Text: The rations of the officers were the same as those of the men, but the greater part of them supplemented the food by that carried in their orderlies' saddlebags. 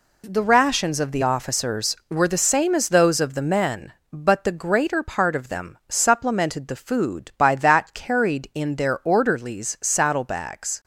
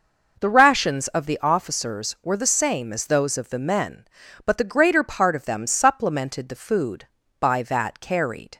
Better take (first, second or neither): first